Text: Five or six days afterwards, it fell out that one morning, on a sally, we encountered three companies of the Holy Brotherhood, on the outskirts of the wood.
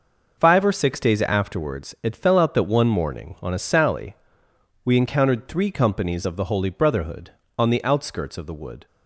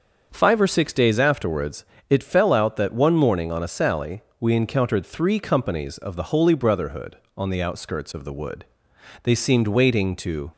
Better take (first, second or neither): first